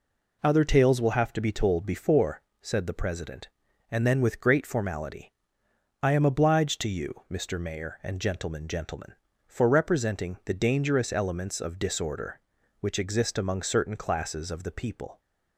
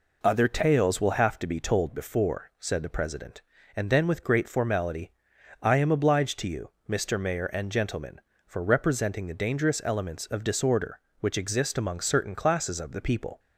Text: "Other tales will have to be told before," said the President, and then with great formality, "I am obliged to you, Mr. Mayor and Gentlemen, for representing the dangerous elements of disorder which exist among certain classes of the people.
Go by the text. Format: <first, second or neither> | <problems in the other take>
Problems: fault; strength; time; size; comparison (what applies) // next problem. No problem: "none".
second | says "Gentlemen" twice; at 8.6 s